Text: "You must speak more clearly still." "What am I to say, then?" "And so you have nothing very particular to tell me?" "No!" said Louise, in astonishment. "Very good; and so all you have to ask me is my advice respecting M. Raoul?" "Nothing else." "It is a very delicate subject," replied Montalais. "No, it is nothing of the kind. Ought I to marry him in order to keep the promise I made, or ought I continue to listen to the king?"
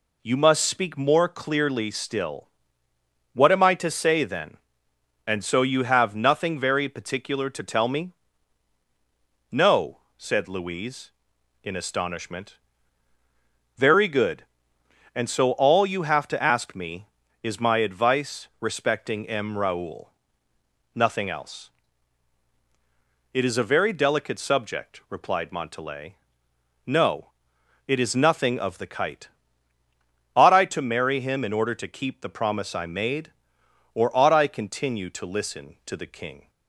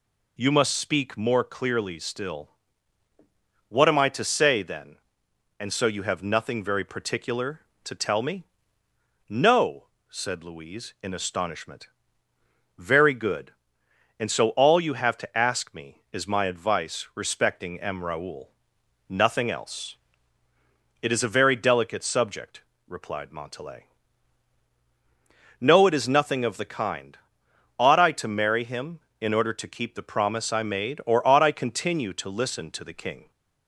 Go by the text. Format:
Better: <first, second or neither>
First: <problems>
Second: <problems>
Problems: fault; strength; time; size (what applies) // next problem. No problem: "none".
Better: second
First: says "kite" for "kind"; at 28.8 s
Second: none